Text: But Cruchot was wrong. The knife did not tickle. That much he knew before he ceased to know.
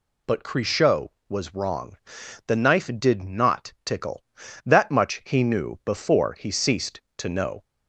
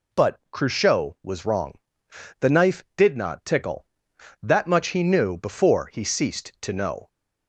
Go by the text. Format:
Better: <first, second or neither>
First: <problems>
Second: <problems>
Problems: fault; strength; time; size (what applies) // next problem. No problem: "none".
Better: neither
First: none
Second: none